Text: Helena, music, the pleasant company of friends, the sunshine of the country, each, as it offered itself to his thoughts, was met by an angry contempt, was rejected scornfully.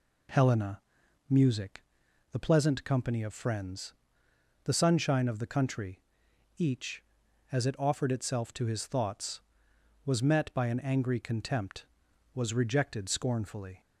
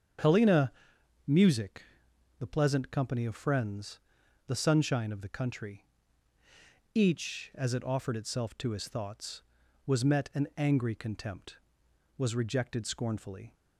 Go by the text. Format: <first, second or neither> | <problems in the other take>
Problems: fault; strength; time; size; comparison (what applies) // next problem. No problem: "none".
first | starts louder than the rest; strong; until 1.7 s; 7.5 dB // skips "by"; at 10.3 s